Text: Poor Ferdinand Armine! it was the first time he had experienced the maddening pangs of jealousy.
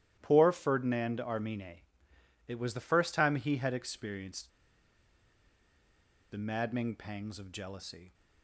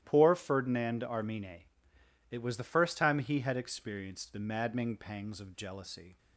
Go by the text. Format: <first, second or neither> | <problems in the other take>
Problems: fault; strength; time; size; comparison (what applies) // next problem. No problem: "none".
second | starts louder than the rest; strong; until 1.2 s; 12.5 dB; strong in the second // pauses between "experienced" and "the"; strong; at 4.4 s; 1.8 s long